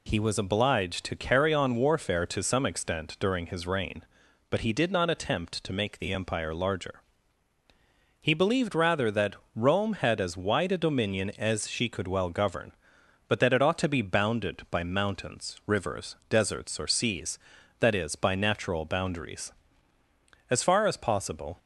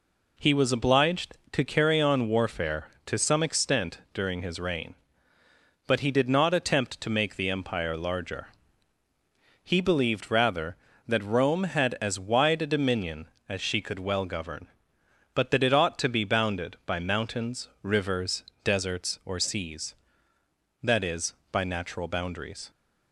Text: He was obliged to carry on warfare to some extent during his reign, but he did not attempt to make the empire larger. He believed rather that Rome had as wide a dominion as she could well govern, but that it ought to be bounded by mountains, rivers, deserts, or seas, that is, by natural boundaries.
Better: second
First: pauses between "that" and "Rome"; slight; at 9.3 s; 0.22 s long // goes on to say "As far as possible"; noticeable; from 20.4 s on; 1.1 s long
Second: none

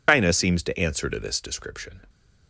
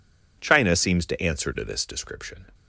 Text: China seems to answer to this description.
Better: second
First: loses the start of "China"; at 0.0 s; 110 ms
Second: none

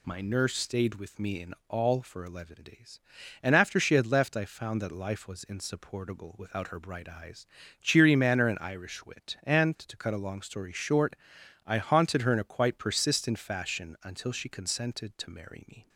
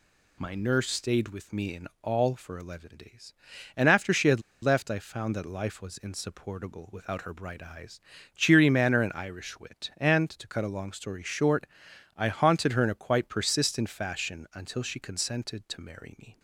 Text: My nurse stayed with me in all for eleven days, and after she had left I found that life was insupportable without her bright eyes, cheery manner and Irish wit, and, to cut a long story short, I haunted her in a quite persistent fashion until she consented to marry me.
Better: first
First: none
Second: pauses between "had" and "left"; slight; at 4.3 s; 0.23 s long

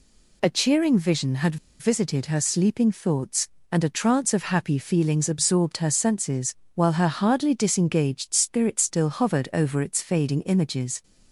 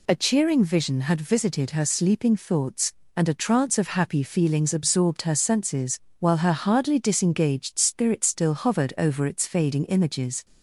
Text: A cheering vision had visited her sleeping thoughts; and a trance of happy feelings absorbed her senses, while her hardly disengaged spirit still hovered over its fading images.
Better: second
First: pauses between "had" and "visited"; slight; at 1.5 s; 0.24 s long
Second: none

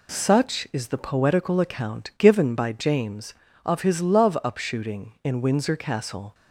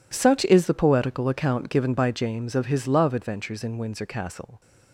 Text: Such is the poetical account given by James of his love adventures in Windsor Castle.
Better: second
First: says "upshooting" for "adventures"; at 4.4 s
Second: none

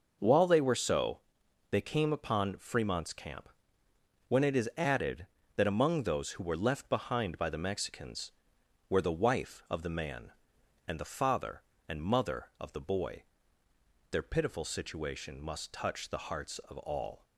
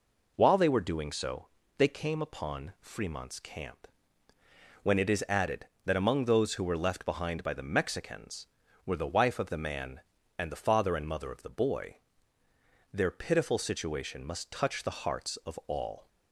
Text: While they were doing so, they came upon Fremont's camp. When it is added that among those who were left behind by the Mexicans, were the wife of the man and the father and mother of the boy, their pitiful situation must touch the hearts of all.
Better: second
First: skips "doing"; at 0.7 s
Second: none

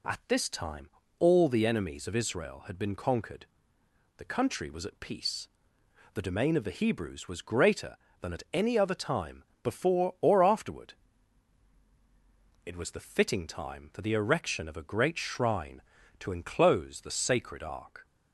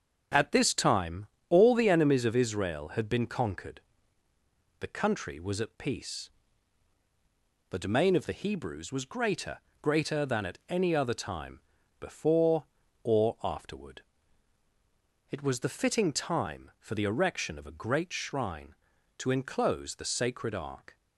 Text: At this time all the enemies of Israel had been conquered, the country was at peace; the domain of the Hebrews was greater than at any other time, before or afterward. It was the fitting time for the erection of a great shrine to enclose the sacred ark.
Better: first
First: pauses between "time" and "all"; slight; at 0.8 s; 0.28 s long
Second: starts louder than the rest; until 1.5 s; 7 dB // pauses between "time" and "all"; slight; at 1.2 s; 0.24 s long // says "greater" twice; at 9.8 s

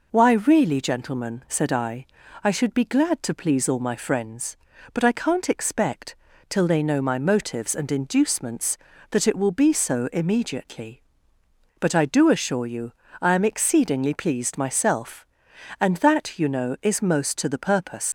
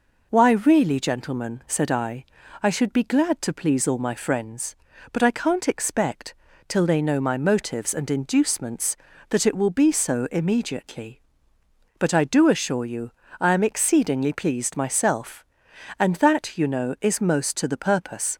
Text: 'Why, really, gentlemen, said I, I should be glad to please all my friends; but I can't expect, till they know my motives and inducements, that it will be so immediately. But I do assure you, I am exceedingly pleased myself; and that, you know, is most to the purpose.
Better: second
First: leaves "purpose" unfinished; at 18.0 s; 70 ms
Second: none

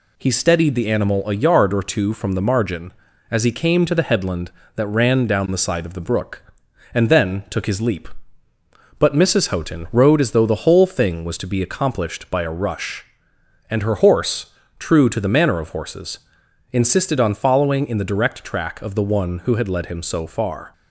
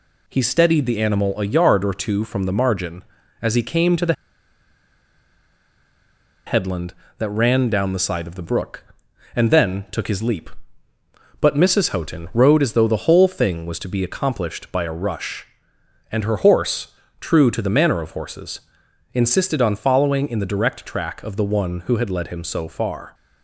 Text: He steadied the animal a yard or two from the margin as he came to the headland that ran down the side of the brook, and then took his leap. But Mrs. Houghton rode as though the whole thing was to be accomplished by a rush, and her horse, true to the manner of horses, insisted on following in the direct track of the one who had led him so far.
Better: first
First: none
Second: pauses between "the" and "headland"; strong; at 4.1 s; 2.3 s long

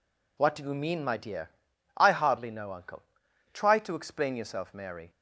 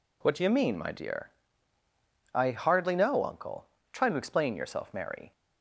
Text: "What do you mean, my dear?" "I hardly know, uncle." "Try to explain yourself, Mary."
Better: neither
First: none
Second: none

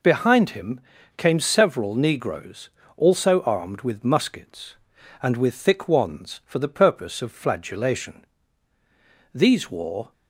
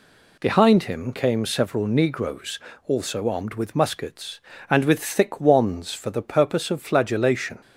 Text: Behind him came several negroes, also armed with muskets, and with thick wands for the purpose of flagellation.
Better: second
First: pauses between "him" and "came"; slight; at 0.7 s; 0.36 s long // goes on to say "These wore"; noticeable; from 9.3 s on; 0.80 s long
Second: none

